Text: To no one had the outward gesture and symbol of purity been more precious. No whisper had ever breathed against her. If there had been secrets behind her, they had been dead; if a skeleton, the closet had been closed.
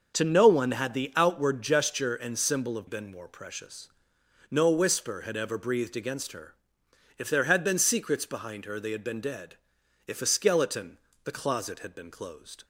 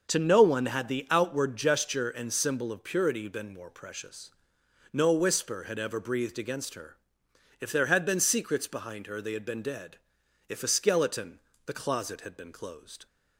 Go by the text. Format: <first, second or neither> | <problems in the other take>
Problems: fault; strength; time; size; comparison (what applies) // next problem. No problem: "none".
second | skips "purity"; at 2.8 s